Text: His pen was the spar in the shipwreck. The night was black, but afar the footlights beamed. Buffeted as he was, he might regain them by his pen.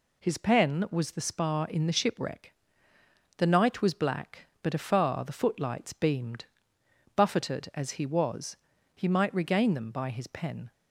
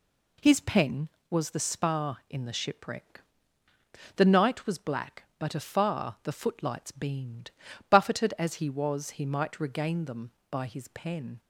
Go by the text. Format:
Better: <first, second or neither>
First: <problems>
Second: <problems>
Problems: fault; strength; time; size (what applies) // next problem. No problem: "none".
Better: neither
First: none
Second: none